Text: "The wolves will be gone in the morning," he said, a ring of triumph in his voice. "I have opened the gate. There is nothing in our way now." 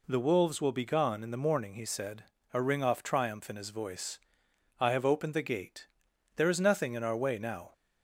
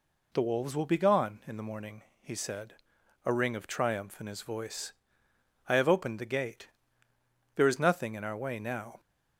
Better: second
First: says "off" for "of"; at 2.8 s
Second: none

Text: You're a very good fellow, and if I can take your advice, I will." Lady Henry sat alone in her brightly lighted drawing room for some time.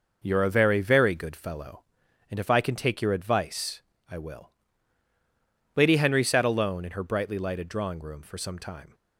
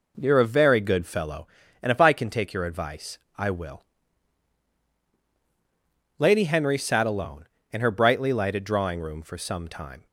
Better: second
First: says "very" twice; at 0.8 s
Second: none

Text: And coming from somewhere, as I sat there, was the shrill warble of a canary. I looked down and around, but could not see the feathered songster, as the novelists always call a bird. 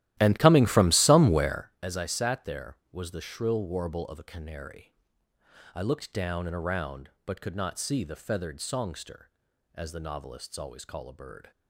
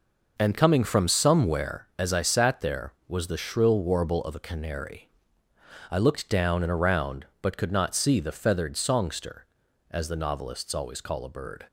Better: second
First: starts louder than the rest; strong; until 1.8 s; 14.5 dB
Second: none

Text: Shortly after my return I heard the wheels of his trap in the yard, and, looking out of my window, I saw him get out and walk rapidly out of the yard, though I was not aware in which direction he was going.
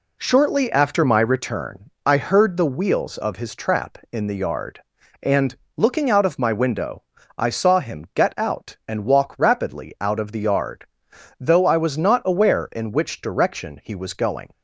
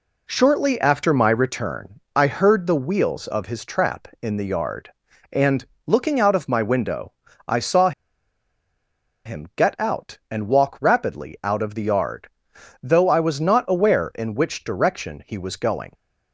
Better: first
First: none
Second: pauses between "saw" and "him"; strong; at 7.9 s; 1.3 s long

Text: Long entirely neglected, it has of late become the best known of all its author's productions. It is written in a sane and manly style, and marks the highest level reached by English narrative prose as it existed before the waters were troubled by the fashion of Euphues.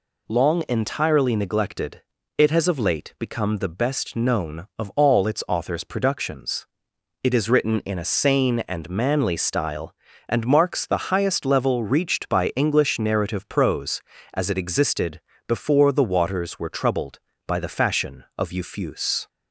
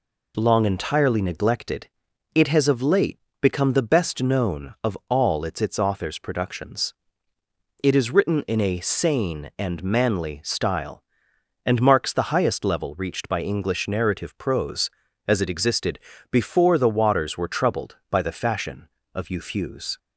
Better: first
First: pauses between "existed" and "before"; slight; at 15.1 s; 0.26 s long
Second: pauses between "late" and "become"; slight; at 3.1 s; 0.22 s long // says "its" twice; at 5.6 s // pauses between "existed" and "before"; slight; at 15.9 s; 0.32 s long

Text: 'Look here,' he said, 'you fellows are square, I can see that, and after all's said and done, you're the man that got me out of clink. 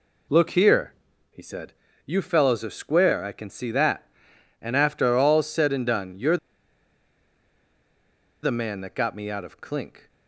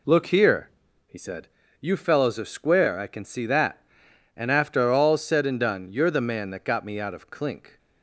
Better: second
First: pauses between "you're" and "the"; strong; at 6.3 s; 2.0 s long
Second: none

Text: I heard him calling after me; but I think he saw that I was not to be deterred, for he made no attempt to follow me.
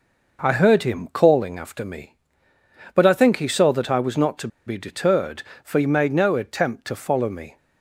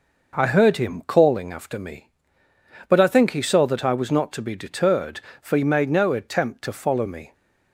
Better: second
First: pauses between "to" and "be"; slight; at 4.4 s; 0.18 s long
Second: none

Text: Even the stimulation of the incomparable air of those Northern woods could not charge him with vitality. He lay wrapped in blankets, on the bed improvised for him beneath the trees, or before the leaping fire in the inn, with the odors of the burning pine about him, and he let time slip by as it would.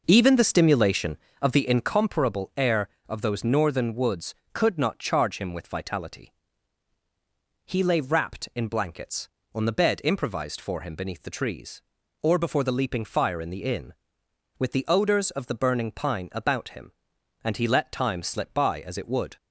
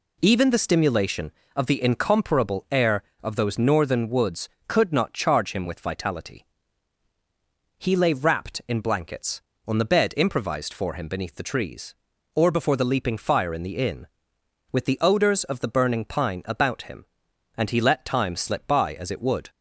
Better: second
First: starts louder than the rest; noticeable; until 1.9 s; 5.5 dB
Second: none

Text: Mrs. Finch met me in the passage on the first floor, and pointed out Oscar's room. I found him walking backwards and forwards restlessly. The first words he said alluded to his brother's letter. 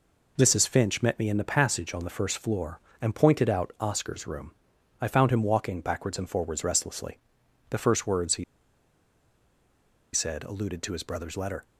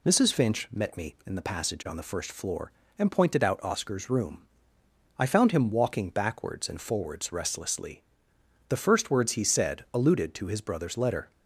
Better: second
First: pauses between "he" and "said"; strong; at 8.4 s; 1.6 s long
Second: none

